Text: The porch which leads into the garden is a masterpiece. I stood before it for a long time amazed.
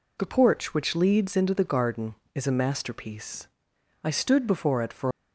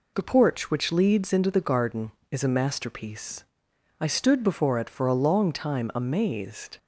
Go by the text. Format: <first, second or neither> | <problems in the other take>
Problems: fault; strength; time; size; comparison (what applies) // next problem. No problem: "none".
second | stops before "a long time amazed"; at 5.1 s